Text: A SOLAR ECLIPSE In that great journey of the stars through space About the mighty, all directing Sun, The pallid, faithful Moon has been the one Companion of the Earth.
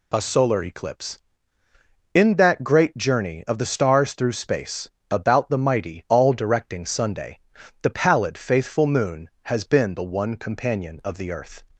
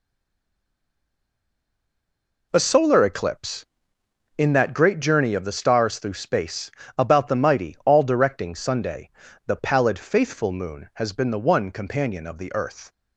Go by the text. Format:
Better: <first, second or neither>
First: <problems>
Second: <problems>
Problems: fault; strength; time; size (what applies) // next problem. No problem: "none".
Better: first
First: pauses between "space" and "About"; slight; at 4.9 s; 0.20 s long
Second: stays silent before the first word; until 2.5 s; 2.5 s long // pauses between "space" and "About"; slight; at 6.7 s; 0.26 s long